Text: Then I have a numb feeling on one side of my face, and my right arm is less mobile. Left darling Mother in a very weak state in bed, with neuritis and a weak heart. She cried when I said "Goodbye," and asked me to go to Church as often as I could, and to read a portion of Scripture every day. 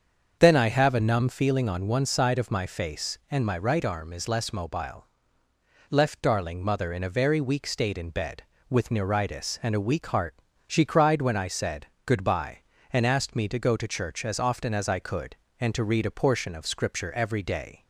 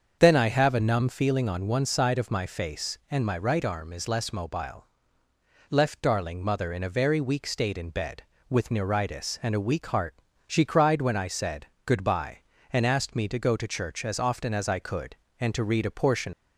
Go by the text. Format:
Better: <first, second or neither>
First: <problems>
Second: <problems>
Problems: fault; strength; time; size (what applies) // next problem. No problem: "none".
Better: first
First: starts louder than the rest; until 1.4 s; 7 dB // pauses between "said" and "Goodbye"; slight; at 11.8 s; 0.18 s long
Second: starts louder than the rest; until 1.2 s; 7 dB // pauses between "said" and "Goodbye"; slight; at 11.6 s; 0.18 s long // stops before "of Scripture every day"; at 16.3 s